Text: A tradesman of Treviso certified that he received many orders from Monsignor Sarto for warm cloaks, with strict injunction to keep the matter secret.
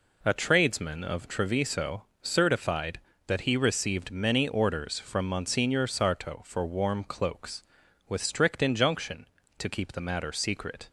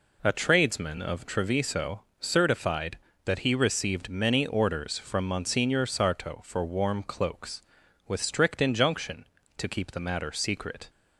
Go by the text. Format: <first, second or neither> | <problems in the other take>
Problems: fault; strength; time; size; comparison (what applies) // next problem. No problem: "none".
neither | pauses between "Treviso" and "certified"; slight; the same in both